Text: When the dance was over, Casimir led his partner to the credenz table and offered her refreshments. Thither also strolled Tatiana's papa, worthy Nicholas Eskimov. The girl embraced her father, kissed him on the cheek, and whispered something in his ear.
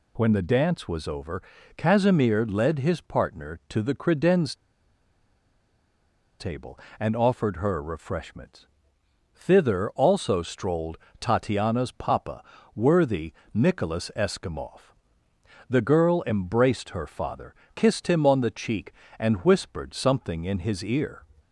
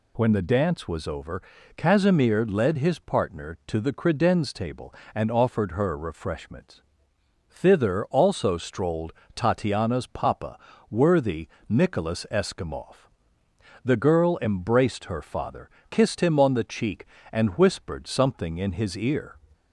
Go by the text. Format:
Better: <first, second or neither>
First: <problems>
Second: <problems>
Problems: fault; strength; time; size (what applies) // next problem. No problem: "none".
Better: second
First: pauses between "credenz" and "table"; strong; at 4.5 s; 1.8 s long // pauses between "strolled" and "Tatiana's"; slight; at 10.9 s; 0.22 s long // pauses between "worthy" and "Nicholas"; slight; at 13.3 s; 0.20 s long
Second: pauses between "strolled" and "Tatiana's"; slight; at 9.1 s; 0.22 s long // pauses between "worthy" and "Nicholas"; slight; at 11.4 s; 0.20 s long